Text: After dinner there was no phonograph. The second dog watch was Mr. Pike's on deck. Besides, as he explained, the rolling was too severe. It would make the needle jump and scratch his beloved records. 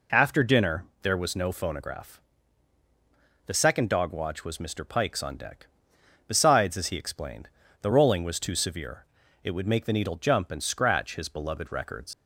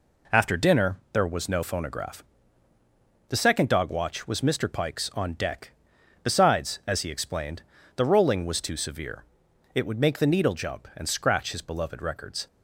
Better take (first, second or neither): second